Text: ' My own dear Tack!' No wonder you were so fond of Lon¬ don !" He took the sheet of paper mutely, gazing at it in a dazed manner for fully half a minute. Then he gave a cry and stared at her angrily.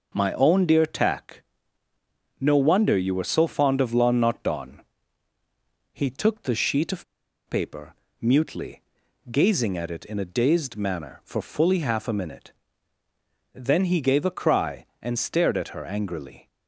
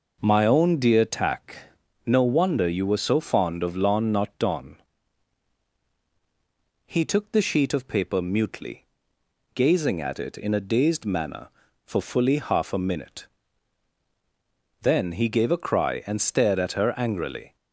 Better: second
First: starts louder than the rest; noticeable; until 1.1 s; 6 dB // pauses between "of" and "paper"; at 7.0 s; 0.44 s long // pauses between "paper" and "mutely"; slight; at 7.9 s; 0.28 s long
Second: starts louder than the rest; until 1.2 s; 6 dB

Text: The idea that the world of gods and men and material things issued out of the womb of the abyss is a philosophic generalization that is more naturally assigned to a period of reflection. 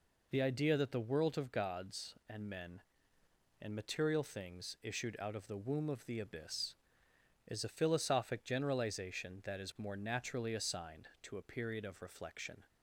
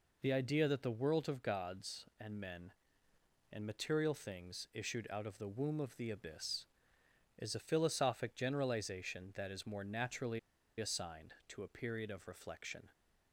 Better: first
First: none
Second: pauses between "naturally" and "assigned"; at 10.3 s; 0.40 s long

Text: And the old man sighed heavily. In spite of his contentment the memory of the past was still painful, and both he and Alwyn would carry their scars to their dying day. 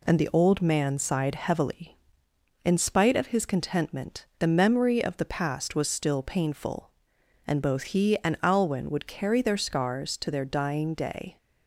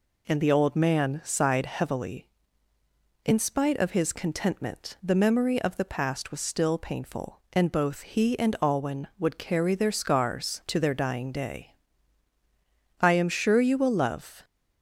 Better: first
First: none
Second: goes on to say "I am sure you will love"; from 12.9 s on; 1.4 s long

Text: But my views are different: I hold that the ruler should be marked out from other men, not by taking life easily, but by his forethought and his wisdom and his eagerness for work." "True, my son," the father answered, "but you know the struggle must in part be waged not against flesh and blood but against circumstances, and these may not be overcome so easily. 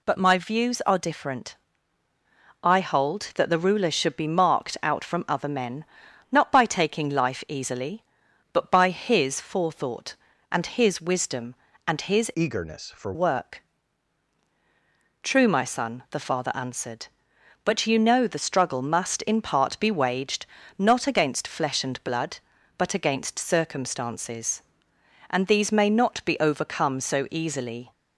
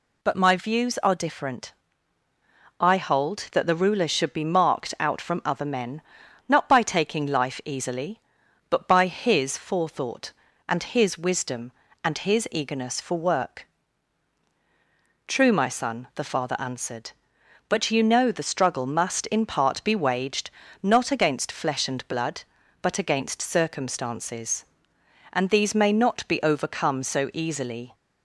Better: second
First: changes voice from "eagerness" to "for"; from 12.3 to 13.1 s; 0.8 s long // pauses between "waged" and "not"; slight; at 20.4 s; 0.32 s long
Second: pauses between "waged" and "not"; slight; at 20.4 s; 0.32 s long

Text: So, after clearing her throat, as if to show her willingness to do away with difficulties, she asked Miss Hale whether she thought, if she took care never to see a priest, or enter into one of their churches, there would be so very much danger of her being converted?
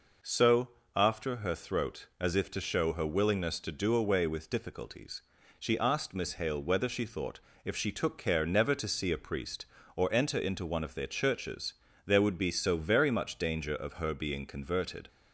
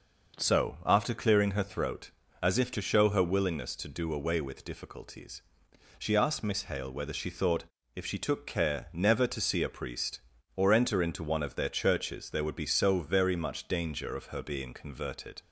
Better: second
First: skips "clearing"; at 1.3 s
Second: none

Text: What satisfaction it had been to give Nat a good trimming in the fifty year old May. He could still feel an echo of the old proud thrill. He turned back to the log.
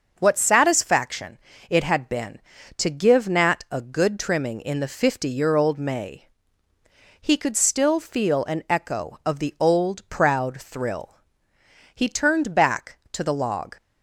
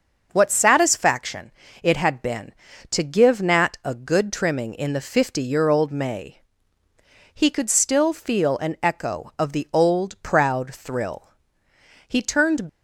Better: first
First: starts louder than the rest; until 1.1 s; 6 dB // pauses between "satisfaction" and "it"; slight; at 1.3 s; 0.30 s long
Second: starts louder than the rest; until 1.3 s; 6 dB // pauses between "satisfaction" and "it"; slight; at 1.5 s; 0.30 s long // stops before "back to the log"; at 12.6 s

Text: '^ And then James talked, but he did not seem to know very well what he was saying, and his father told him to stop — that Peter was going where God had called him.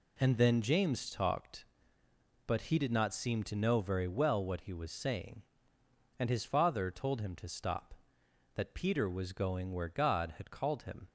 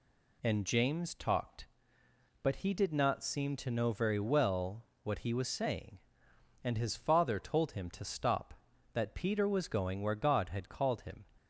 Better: first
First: none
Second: skips "then"; at 0.6 s // pauses between "well" and "what"; slight; at 4.8 s; 0.16 s long

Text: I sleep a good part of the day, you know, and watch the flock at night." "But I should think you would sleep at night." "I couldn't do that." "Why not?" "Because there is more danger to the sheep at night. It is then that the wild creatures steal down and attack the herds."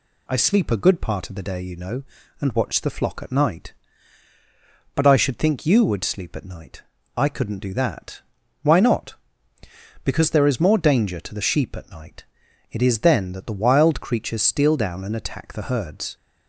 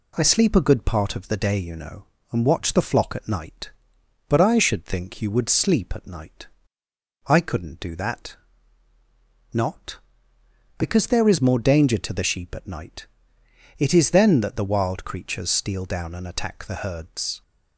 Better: first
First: none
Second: skips "Why"; at 8.9 s

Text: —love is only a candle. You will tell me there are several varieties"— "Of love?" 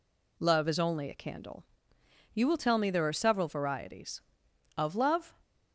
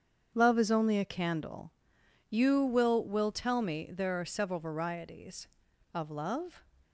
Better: first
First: none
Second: starts louder than the rest; strong; until 1.3 s; 7.5 dB // says "will" twice; at 3.0 s

